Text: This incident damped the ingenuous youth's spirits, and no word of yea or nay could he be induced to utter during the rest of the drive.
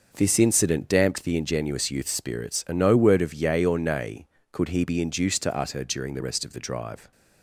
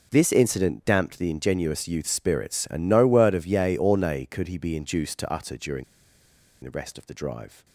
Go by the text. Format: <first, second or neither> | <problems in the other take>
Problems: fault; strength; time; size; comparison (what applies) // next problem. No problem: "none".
first | pauses between "during" and "the"; noticeable; at 5.8 s; 0.80 s long